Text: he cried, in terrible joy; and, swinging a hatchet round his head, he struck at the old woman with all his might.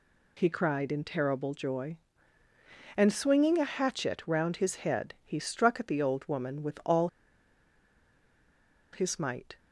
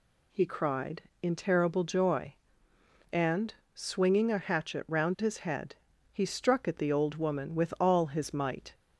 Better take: second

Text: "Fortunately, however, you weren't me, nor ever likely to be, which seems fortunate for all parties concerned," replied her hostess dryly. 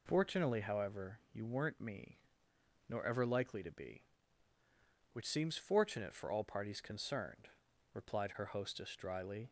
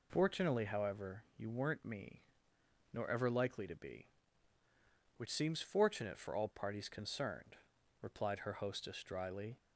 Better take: neither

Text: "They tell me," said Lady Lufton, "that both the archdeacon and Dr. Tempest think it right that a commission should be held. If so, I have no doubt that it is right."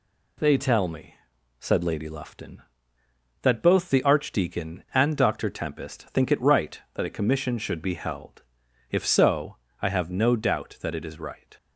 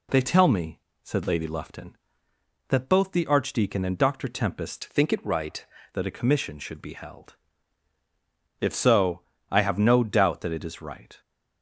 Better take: first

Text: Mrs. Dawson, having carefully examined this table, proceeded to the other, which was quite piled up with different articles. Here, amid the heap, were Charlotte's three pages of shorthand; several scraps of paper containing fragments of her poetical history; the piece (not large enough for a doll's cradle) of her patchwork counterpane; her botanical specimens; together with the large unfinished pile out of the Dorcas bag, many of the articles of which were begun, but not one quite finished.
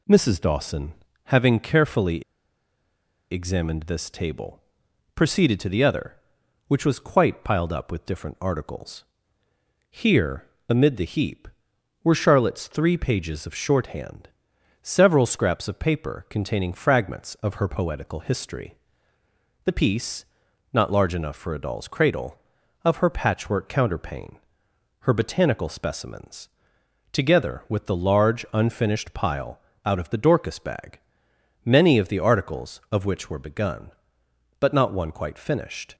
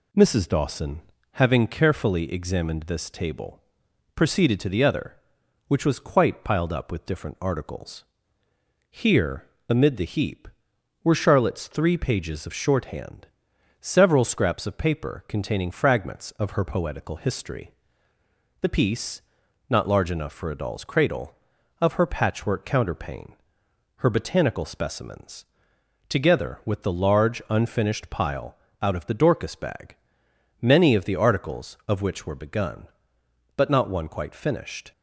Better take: second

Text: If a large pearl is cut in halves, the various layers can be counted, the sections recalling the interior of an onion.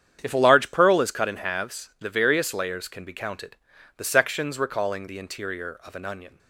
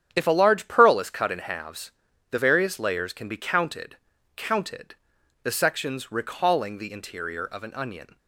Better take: first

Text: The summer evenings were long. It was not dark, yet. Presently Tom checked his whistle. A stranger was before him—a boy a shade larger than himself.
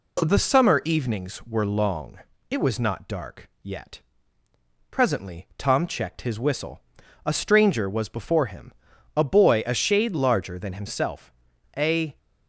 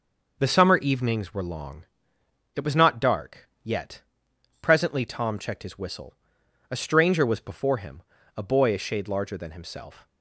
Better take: second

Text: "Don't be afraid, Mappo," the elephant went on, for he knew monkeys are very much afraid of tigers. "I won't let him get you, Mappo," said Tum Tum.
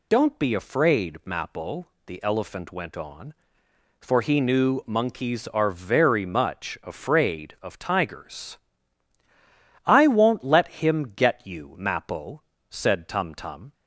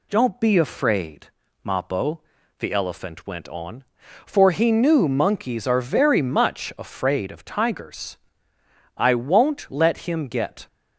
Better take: first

